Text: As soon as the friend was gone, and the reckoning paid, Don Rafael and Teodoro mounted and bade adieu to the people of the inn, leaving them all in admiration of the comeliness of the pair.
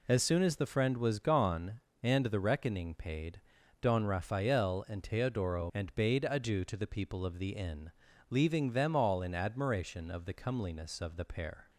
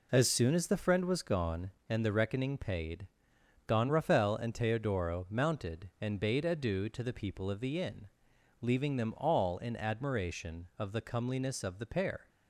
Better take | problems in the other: second | skips "mounted"; at 5.7 s

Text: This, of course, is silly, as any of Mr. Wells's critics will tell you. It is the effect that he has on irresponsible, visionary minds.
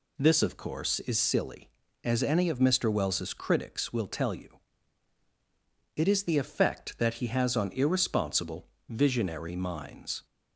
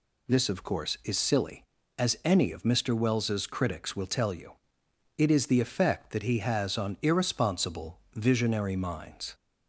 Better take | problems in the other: neither | none

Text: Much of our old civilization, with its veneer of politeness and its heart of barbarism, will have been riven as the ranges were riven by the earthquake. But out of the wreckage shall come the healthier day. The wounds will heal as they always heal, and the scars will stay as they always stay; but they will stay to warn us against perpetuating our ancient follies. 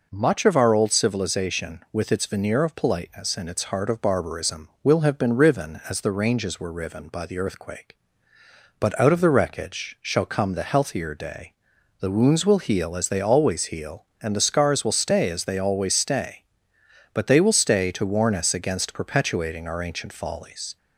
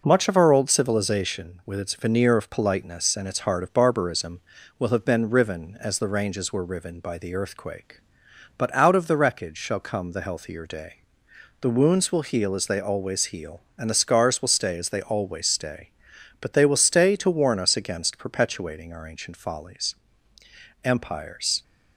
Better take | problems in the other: first | goes on to say "Empires"; noticeable; from 20.8 s on; 0.78 s long

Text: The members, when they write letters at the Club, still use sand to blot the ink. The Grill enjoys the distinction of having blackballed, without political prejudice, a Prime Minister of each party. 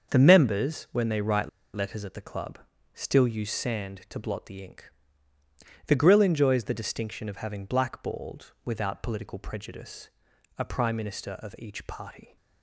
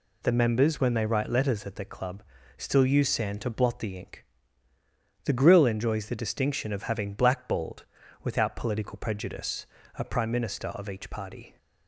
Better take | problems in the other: second | starts louder than the rest; until 1.1 s; 6.5 dB // pauses between "write" and "letters"; slight; at 1.4 s; 0.26 s long

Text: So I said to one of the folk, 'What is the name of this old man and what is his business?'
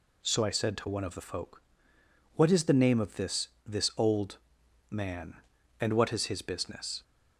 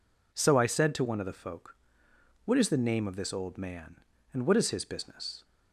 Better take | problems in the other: second | says "this" twice; at 3.6 s // pauses between "old" and "man"; noticeable; at 4.3 s; 0.54 s long

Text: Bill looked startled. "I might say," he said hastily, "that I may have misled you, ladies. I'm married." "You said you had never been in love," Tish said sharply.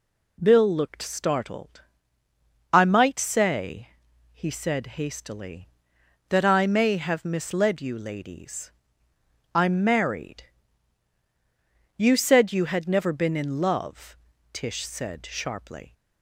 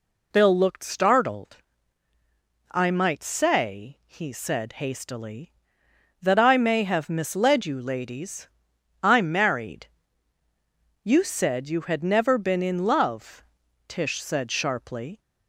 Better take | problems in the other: neither | none

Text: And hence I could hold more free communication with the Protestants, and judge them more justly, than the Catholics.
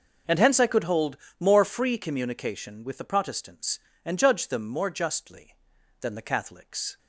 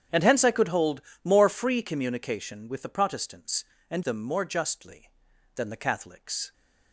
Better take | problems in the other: first | starts louder than the rest; strong; until 1.3 s; 8.5 dB // pauses between "hold" and "more"; slight; at 1.0 s; 0.22 s long; slight in the first // skips "judge"; at 4.0 s

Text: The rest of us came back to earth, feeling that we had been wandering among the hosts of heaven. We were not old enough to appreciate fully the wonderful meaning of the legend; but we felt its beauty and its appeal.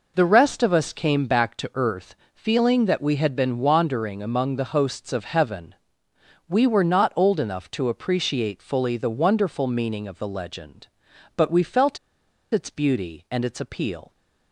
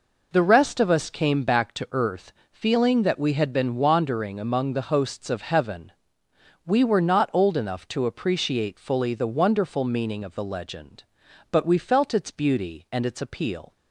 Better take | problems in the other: second | pauses between "felt" and "its"; noticeable; at 11.9 s; 0.55 s long

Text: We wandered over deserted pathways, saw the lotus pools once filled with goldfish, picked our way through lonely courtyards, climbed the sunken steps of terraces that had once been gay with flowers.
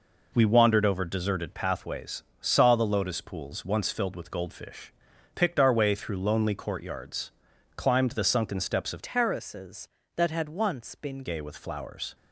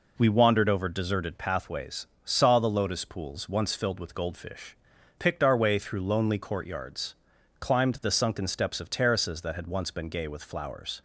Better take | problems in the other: second | changes voice from "terraces" to "been"; from 9.0 to 11.2 s; 2.2 s long

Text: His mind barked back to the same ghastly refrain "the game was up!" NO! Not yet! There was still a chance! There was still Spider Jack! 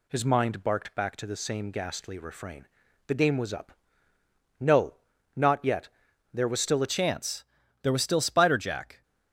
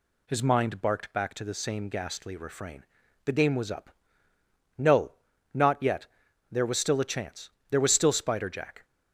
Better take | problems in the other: second | pauses between "refrain" and "the"; at 2.6 s; 0.40 s long; also in the second // changes voice at "chance"; from 6.8 s on; 2.2 s long

